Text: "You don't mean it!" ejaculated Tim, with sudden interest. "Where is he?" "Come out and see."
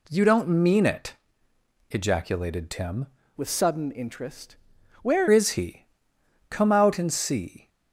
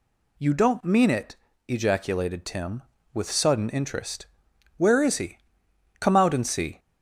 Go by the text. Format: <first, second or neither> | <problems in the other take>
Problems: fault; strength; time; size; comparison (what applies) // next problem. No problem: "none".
second | changes voice from "with" to "Where"; from 3.3 to 5.2 s; 1.9 s long